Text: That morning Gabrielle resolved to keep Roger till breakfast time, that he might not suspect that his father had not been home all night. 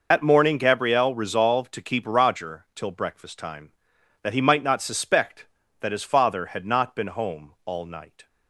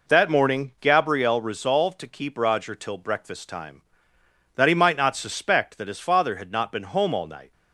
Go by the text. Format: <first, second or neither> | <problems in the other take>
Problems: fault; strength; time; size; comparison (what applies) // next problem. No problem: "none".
second | loses the start of "That"; at 0.1 s; 100 ms